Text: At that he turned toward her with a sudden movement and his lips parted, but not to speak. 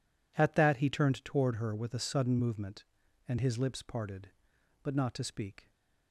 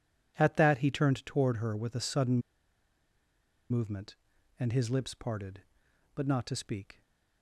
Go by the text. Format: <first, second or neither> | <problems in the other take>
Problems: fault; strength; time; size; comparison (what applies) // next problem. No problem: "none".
first | pauses between "sudden" and "movement"; strong; at 2.3 s; 1.3 s long